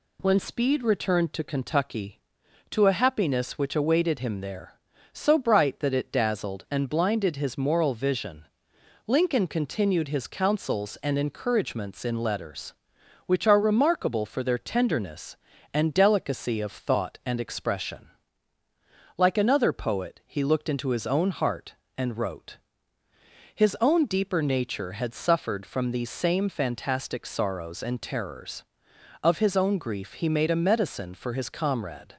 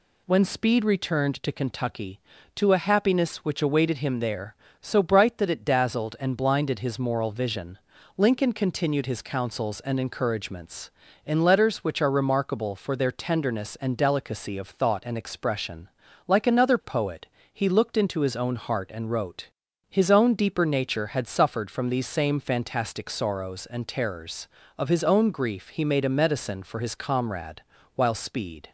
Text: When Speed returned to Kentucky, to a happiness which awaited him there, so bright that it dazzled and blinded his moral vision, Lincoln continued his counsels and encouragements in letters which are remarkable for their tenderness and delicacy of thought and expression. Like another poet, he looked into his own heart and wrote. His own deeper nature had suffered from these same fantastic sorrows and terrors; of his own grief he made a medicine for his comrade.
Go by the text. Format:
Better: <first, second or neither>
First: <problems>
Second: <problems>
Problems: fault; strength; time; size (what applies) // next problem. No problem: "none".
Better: first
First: none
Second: goes on to say "While Speed"; noticeable; from 27.9 s on; 0.76 s long